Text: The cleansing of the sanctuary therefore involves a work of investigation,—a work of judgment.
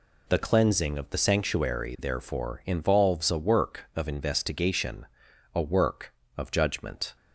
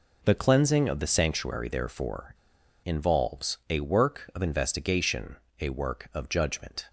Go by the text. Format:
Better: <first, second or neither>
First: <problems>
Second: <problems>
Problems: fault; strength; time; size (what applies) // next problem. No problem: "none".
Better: first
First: none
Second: pauses between "therefore" and "involves"; noticeable; at 2.3 s; 0.47 s long